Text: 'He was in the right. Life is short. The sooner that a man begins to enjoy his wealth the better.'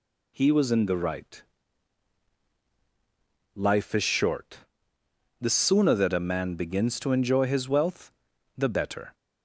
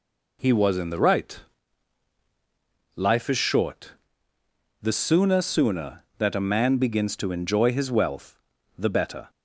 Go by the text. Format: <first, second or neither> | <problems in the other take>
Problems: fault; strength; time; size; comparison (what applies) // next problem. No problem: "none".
first | says "sooner" twice; at 5.4 s // pauses between "wealth" and "the"; at 8.3 s; 0.40 s long; noticeable in the first